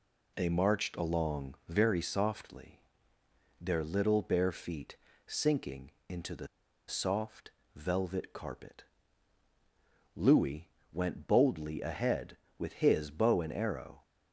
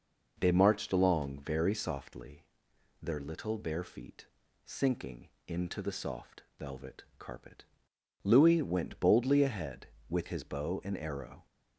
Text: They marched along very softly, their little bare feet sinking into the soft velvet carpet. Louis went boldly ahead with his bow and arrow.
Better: second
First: pauses between "feet" and "sinking"; slight; at 4.9 s; 0.32 s long // pauses between "sinking" and "into"; slight; at 5.9 s; 0.18 s long // pauses between "the" and "soft"; at 6.4 s; 0.40 s long // pauses between "soft" and "velvet"; slight; at 7.5 s; 0.24 s long // pauses between "Louis" and "went"; slight; at 10.6 s; 0.24 s long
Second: pauses between "feet" and "sinking"; at 4.2 s; 0.38 s long // pauses between "sinking" and "into"; slight; at 5.2 s; 0.18 s long // pauses between "soft" and "velvet"; slight; at 6.4 s; 0.16 s long

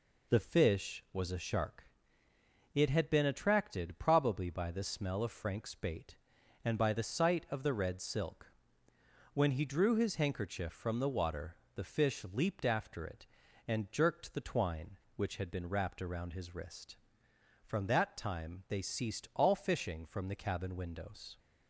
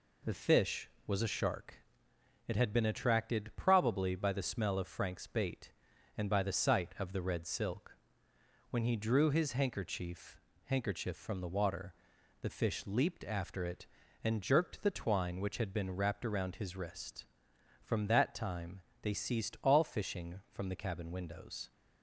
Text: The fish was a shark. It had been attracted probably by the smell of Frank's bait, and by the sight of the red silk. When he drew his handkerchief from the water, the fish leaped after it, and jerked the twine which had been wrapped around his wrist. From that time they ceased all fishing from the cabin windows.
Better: first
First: none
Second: says "handkerchief" twice; at 10.6 s // pauses between "time" and "they"; slight; at 18.8 s; 0.20 s long

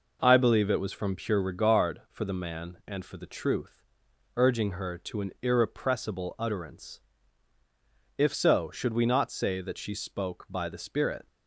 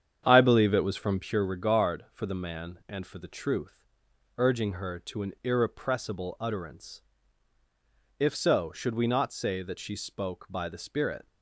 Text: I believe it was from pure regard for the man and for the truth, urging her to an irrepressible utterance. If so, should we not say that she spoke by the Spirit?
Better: first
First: none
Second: starts louder than the rest; strong; until 1.4 s; 8.5 dB

